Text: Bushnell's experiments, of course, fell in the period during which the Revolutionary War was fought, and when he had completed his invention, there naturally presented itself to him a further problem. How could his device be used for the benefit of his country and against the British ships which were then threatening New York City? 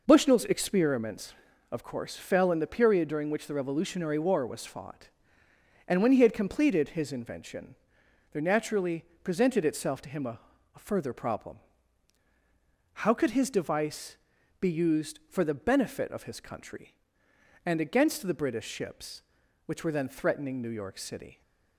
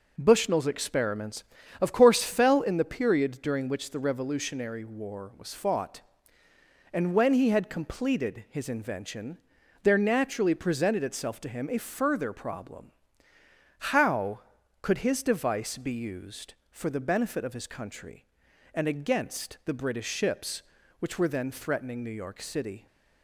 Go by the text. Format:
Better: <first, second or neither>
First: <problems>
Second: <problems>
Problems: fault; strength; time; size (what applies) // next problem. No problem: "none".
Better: second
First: pauses between "naturally" and "presented"; slight; at 9.0 s; 0.18 s long // says "a" twice; at 10.7 s // pauses between "device" and "be"; noticeable; at 14.1 s; 0.46 s long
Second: none